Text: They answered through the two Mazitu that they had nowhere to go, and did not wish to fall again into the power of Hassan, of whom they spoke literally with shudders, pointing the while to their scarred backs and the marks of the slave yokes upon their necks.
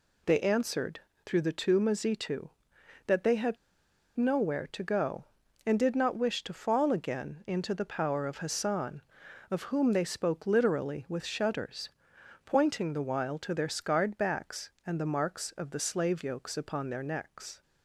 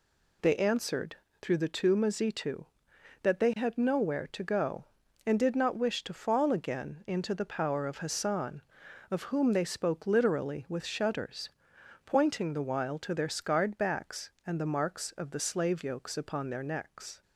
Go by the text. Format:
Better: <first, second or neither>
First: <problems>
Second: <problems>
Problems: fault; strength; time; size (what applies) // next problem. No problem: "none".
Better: second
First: pauses between "answered" and "through"; slight; at 1.0 s; 0.24 s long // pauses between "had" and "nowhere"; noticeable; at 3.5 s; 0.60 s long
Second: pauses between "answered" and "through"; slight; at 1.1 s; 0.24 s long